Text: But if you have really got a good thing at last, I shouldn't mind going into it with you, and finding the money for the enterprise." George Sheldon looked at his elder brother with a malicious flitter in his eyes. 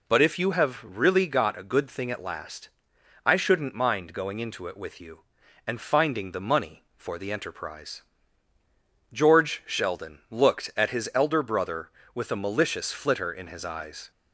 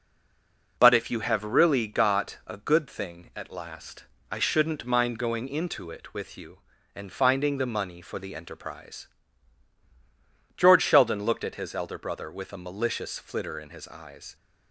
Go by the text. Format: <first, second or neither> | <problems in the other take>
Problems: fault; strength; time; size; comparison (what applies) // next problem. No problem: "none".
first | stays silent before the first word; slight; until 0.7 s; 0.7 s long